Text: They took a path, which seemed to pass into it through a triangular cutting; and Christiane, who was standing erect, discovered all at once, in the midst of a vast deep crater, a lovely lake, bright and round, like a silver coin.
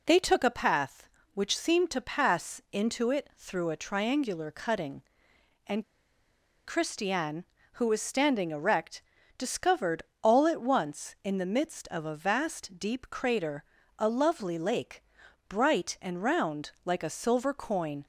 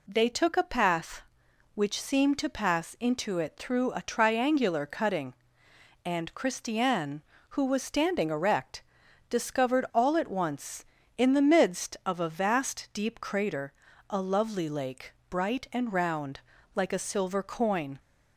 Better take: second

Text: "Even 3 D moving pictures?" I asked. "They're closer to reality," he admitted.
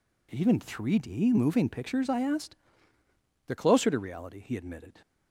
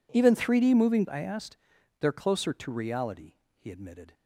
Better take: first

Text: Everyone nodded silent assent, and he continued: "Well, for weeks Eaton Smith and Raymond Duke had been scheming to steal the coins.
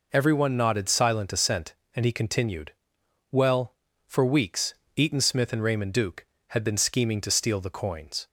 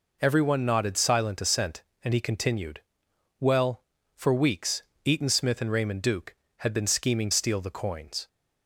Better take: first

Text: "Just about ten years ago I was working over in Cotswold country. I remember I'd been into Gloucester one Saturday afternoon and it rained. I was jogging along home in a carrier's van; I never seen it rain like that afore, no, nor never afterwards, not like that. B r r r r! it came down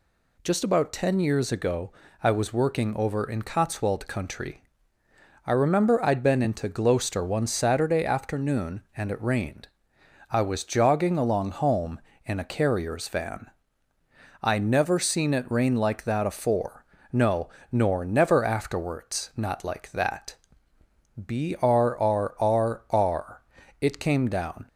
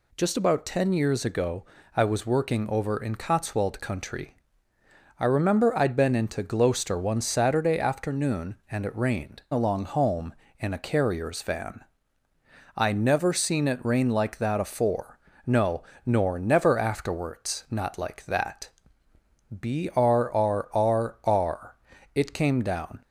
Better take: first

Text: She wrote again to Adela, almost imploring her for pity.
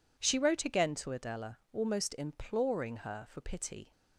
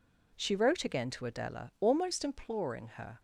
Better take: first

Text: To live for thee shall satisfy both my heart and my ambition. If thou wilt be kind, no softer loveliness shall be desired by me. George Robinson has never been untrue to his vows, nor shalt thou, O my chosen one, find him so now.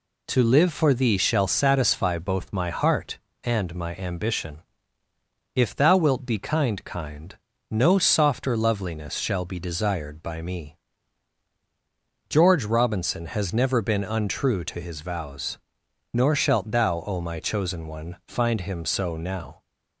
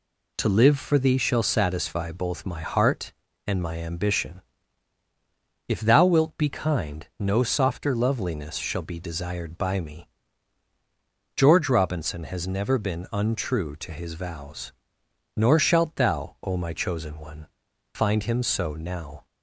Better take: second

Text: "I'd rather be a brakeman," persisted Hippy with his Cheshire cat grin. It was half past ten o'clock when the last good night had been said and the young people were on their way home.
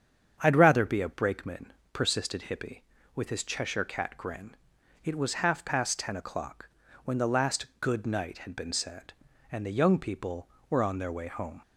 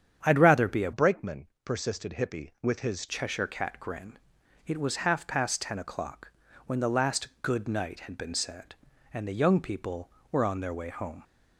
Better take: first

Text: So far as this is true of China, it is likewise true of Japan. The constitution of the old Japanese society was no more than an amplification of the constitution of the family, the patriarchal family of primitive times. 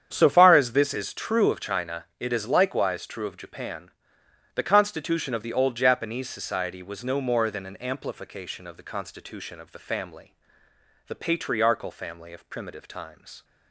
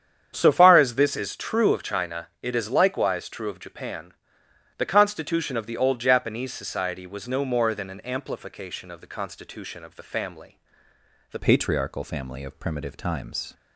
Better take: first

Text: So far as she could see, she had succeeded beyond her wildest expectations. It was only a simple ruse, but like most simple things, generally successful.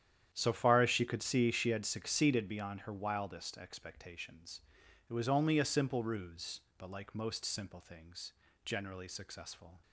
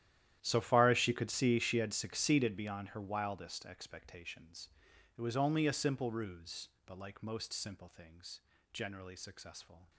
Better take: first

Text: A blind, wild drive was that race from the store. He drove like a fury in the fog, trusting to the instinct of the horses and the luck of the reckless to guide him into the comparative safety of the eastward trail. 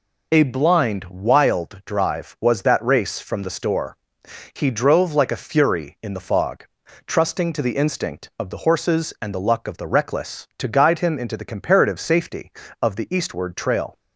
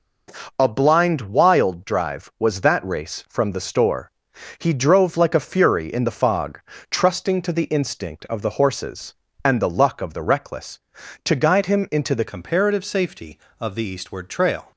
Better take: first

